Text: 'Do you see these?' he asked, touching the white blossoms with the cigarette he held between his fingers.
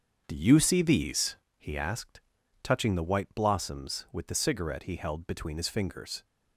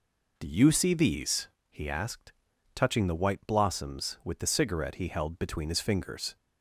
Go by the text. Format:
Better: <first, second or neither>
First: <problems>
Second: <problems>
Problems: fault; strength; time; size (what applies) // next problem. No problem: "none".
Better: second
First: gets quieter; strong; throughout; 7.5 dB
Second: none